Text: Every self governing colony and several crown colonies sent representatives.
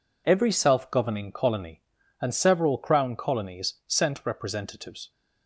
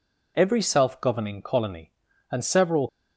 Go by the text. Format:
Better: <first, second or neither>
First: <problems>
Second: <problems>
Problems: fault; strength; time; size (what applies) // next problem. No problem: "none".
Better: first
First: none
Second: stops before "crown colonies sent representatives"; at 2.8 s